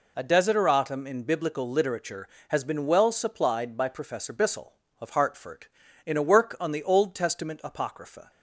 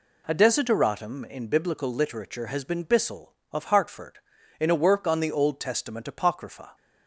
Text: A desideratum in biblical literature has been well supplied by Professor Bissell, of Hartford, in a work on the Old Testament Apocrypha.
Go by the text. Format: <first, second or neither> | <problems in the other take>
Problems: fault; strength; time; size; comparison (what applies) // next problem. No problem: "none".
first | skips "well supplied by Professor"; at 2.8 s